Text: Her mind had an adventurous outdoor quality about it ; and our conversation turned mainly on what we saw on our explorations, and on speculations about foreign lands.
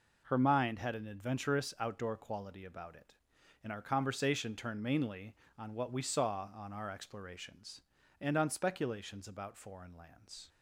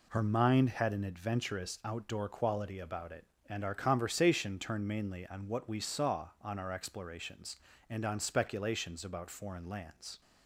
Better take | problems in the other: neither | none

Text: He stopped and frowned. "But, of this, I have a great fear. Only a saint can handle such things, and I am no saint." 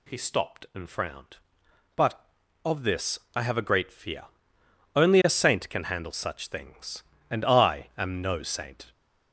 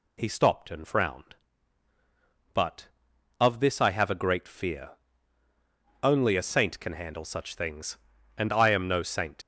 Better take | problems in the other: first | leaves "saint" unfinished; at 9.4 s; 60 ms

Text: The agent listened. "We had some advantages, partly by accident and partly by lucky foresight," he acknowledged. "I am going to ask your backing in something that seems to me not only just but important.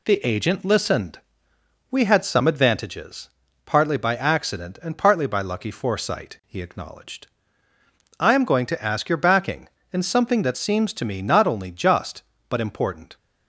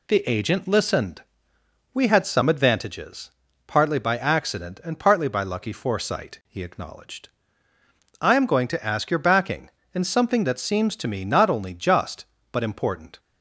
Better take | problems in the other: neither | none

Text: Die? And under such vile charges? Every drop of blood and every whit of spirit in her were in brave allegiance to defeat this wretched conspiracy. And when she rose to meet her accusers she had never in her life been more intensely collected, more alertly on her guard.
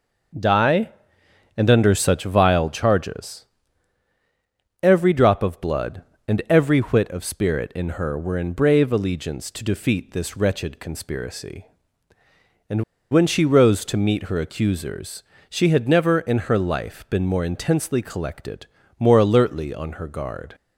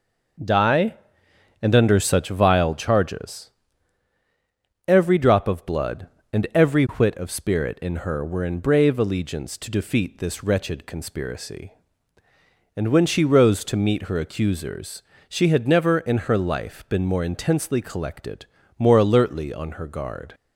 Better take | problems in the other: second | pauses between "And" and "when"; slight; at 12.8 s; 0.29 s long // pauses between "accusers" and "she"; slight; at 15.2 s; 0.30 s long; slight in the second

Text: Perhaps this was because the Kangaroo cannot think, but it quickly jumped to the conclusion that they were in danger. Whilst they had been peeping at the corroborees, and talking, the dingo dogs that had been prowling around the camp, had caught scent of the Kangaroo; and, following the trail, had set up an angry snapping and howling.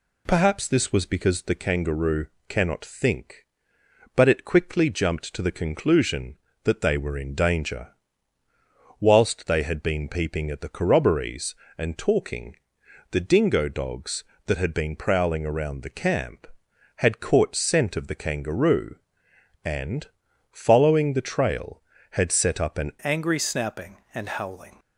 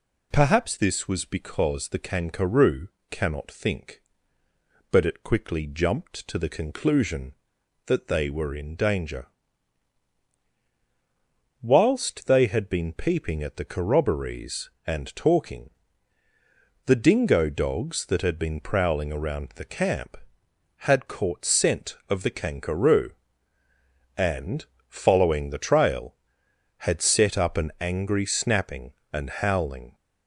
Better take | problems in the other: second | pauses between "Kangaroo" and "cannot"; slight; at 2.2 s; 0.22 s long; slight in the second // changes voice at "angry"; from 22.9 s on; 1.8 s long

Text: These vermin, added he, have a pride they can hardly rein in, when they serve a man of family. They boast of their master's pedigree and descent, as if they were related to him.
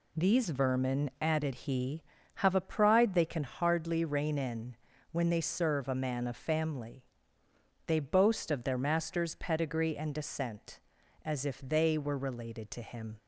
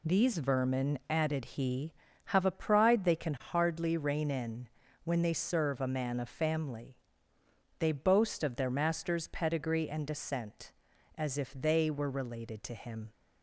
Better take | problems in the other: neither | none

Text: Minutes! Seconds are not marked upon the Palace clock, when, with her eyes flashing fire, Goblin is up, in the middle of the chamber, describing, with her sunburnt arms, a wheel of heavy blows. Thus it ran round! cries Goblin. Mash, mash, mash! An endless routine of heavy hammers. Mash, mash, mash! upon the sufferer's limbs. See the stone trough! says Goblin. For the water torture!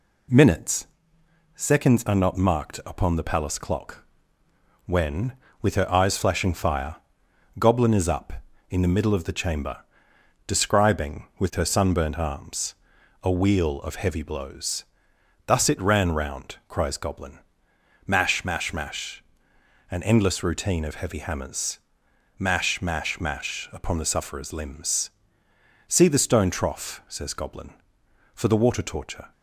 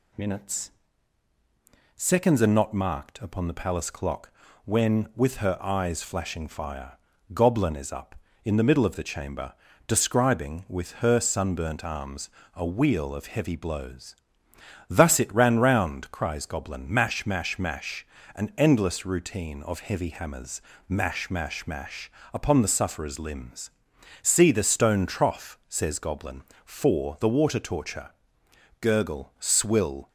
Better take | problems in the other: first | goes on to say "Gurgle swill"; noticeable; from 28.7 s on; 1.2 s long

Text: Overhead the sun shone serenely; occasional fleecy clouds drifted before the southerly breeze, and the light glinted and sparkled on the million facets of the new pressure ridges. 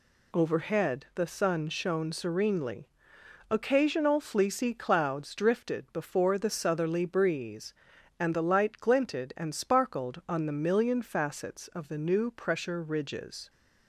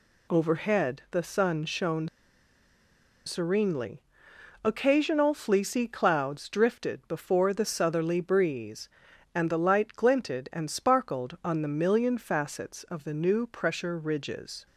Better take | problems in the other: first | pauses between "shone" and "serenely"; at 2.0 s; 1.1 s long

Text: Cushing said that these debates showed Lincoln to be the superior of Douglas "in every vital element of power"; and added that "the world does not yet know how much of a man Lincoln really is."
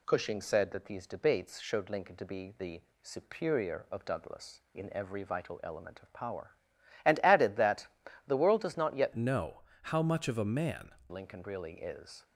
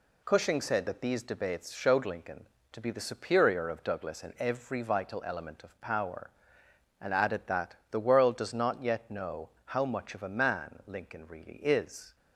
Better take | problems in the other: second | pauses between "the" and "superior"; slight; at 2.8 s; 0.20 s long // pauses between "that" and "the"; at 7.8 s; 0.40 s long; slight in the second // changes voice from "know" to "man"; from 9.1 to 10.9 s; 1.8 s long // pauses between "know" and "how"; slight; at 9.6 s; 0.20 s long; slight in the second

